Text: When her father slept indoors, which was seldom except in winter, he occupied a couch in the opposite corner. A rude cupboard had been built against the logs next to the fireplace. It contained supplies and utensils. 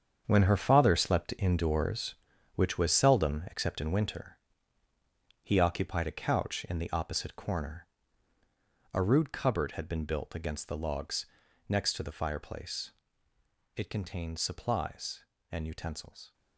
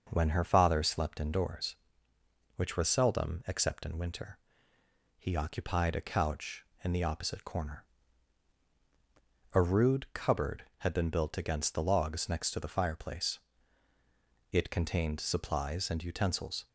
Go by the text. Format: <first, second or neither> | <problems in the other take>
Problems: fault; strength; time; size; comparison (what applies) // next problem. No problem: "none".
second | gets quieter; strong; throughout; 11 dB // starts louder than the rest; strong; until 1.2 s; 7.5 dB; also in the second // pauses between "logs" and "next"; at 11.2 s; 0.42 s long